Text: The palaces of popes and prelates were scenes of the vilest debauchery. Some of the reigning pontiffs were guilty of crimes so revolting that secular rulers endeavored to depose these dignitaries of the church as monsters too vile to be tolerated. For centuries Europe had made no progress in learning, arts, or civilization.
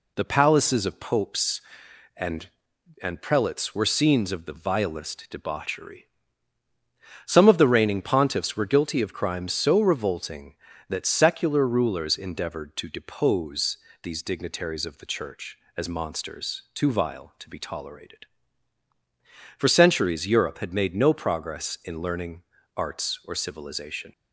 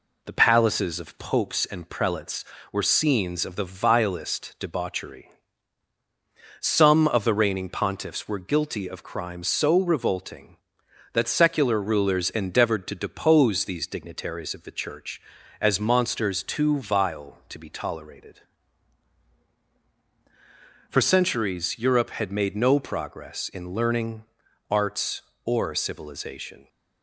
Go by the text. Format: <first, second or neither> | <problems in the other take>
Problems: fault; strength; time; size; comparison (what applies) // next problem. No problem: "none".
second | says "and" twice; at 3.0 s // pauses between "depose" and "these"; slight; at 13.7 s; 0.24 s long